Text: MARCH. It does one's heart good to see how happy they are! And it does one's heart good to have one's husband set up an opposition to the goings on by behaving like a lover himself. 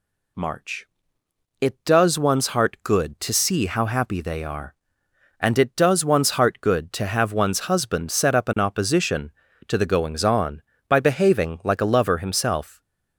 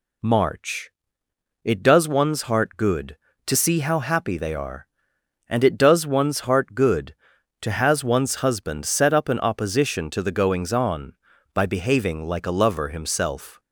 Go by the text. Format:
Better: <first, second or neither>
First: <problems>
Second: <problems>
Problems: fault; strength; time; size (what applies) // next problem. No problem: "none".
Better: first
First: none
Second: says "has" for "have"; at 7.7 s